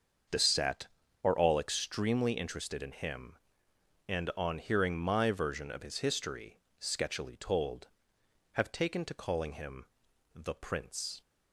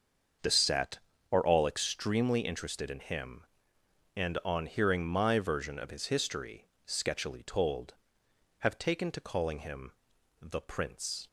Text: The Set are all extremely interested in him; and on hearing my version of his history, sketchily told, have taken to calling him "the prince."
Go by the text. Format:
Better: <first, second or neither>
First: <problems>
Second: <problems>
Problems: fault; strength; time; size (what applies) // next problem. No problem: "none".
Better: neither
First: starts louder than the rest; until 1.6 s; 6.5 dB // pauses between "him" and "the"; noticeable; at 9.8 s; 0.46 s long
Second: starts louder than the rest; until 1.7 s; 6.5 dB // pauses between "him" and "the"; noticeable; at 9.9 s; 0.46 s long